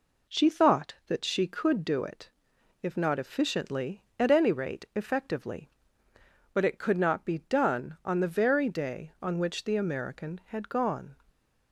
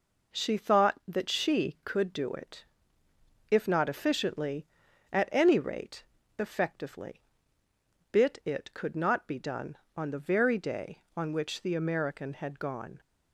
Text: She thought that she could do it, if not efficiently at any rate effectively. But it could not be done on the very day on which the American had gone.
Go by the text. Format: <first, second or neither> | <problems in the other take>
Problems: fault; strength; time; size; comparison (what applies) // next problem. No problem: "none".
first | pauses between "rate" and "effectively"; slight; at 6.0 s; 0.34 s long // says "Bit" for "But"; at 8.1 s